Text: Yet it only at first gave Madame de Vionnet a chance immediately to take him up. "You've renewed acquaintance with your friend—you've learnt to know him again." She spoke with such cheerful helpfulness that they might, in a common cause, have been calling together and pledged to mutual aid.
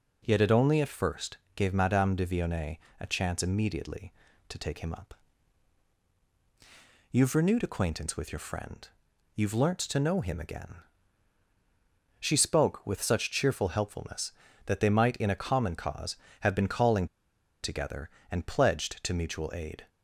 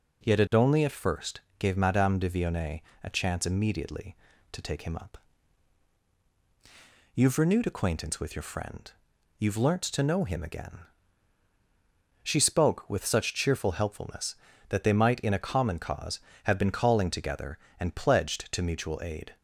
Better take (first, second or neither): second